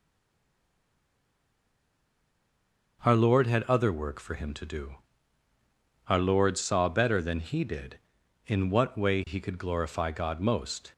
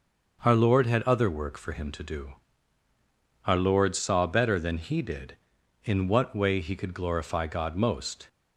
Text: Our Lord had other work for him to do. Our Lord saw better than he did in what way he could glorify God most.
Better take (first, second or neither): second